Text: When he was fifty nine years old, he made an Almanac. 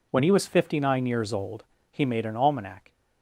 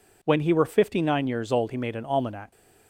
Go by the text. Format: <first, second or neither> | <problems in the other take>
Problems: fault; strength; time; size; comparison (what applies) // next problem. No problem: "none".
first | says "were" for "was"; at 0.5 s